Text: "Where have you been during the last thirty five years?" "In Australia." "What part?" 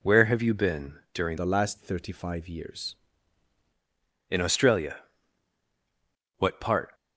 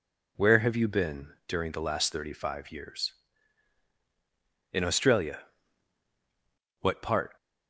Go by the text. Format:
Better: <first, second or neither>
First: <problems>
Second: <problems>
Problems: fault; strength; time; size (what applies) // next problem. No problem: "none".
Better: second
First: pauses between "been" and "during"; slight; at 0.9 s; 0.16 s long // changes voice from "the" to "years"; from 1.3 to 2.9 s; 1.6 s long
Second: pauses between "been" and "during"; slight; at 1.3 s; 0.16 s long